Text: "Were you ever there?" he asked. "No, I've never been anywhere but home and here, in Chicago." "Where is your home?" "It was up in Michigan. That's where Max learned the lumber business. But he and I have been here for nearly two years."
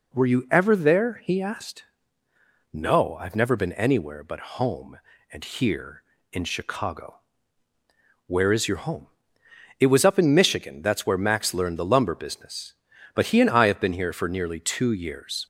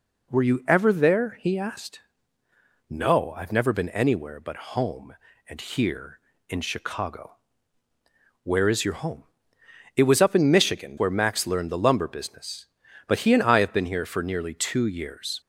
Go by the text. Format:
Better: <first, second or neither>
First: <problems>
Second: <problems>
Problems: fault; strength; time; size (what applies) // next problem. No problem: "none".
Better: first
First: none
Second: skips "That's"; at 10.9 s